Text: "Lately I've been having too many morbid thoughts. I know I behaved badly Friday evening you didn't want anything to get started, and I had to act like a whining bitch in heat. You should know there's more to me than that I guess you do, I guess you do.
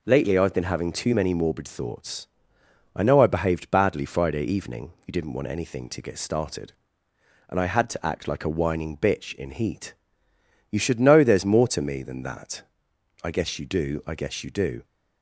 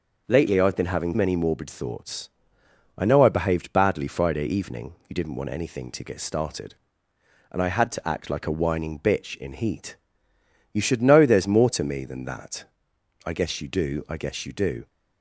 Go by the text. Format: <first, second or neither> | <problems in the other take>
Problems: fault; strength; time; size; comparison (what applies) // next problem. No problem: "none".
first | skips "too"; at 1.1 s // pauses between "that" and "I"; noticeable; at 12.6 s; 0.60 s long; noticeable in the first